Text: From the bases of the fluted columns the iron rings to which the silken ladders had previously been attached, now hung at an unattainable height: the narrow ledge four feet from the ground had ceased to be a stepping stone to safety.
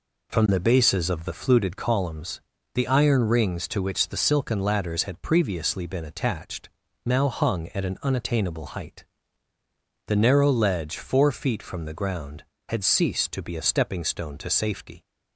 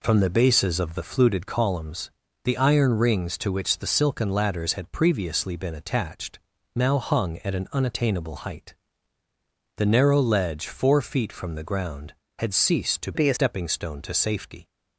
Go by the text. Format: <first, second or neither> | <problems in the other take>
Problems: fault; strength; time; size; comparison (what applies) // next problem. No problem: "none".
first | pauses between "columns" and "the"; slight; at 2.1 s; 0.32 s long; slight in the first // changes voice from "be" to "a"; from 13.1 to 13.3 s; 0.2 s long